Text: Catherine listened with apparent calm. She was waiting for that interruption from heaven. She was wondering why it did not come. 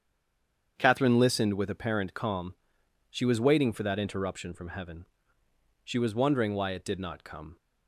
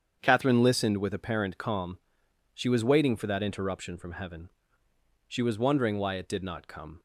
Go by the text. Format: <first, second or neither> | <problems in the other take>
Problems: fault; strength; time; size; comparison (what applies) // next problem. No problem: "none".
second | stays silent before the first word; slight; until 0.7 s; 0.7 s long // starts louder than the rest; strong; until 1.7 s; 8 dB; strong in the second